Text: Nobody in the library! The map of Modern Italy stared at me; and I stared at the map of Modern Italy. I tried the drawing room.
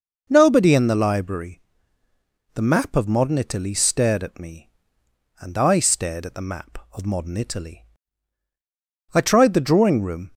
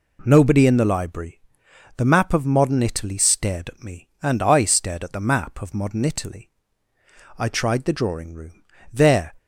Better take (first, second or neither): first